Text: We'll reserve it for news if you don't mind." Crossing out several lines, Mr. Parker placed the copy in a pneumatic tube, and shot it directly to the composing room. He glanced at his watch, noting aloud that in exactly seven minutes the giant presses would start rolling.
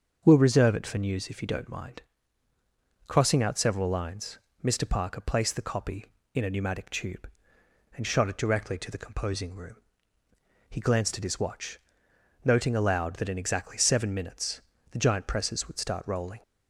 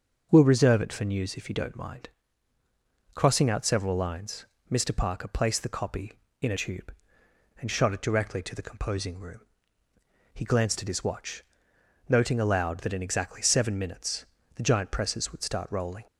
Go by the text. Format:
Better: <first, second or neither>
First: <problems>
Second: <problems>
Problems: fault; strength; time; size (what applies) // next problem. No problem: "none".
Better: first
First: starts louder than the rest; until 1.2 s; 6.5 dB // pauses between "minutes" and "the"; slight; at 14.6 s; 0.30 s long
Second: starts louder than the rest; until 1.3 s; 6.5 dB // skips "pneumatic"; at 6.5 s // pauses between "minutes" and "the"; slight; at 14.2 s; 0.30 s long